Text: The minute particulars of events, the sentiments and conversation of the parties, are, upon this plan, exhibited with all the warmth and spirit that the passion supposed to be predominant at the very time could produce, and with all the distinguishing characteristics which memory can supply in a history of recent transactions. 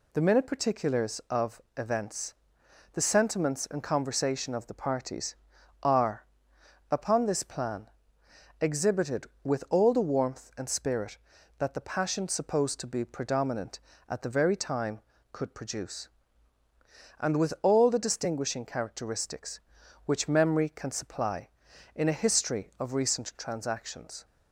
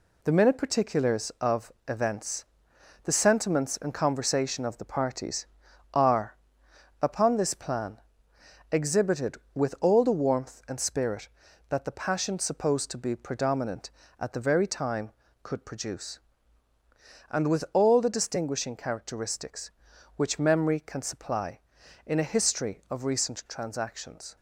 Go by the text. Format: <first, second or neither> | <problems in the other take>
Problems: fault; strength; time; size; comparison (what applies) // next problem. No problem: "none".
first | gets quieter; noticeable; throughout; 6 dB // pauses between "of" and "events"; slight; at 1.7 s; 0.16 s long; slight in the first